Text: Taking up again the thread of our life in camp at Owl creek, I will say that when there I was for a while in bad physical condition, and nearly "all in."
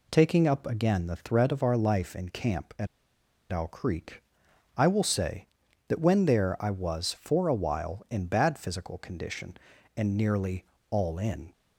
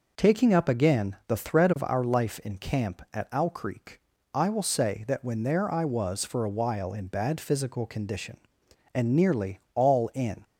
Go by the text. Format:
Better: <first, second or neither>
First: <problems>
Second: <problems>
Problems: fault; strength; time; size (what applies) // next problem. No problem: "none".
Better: second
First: pauses between "at" and "Owl"; noticeable; at 2.8 s; 0.65 s long // pauses between "nearly" and "all"; slight; at 10.6 s; 0.26 s long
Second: pauses between "nearly" and "all"; slight; at 9.5 s; 0.16 s long